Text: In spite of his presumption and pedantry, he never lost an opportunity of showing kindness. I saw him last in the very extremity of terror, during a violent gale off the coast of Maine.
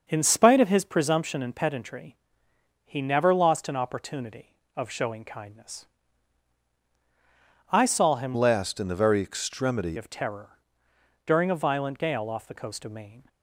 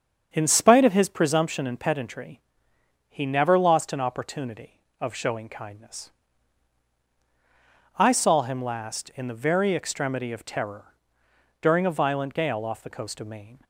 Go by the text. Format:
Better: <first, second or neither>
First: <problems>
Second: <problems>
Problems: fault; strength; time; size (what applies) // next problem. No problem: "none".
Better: second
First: starts louder than the rest; noticeable; until 1.0 s; 6 dB // changes voice from "last" to "extremity"; from 8.3 to 9.9 s; 1.6 s long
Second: starts louder than the rest; strong; until 1.3 s; 7 dB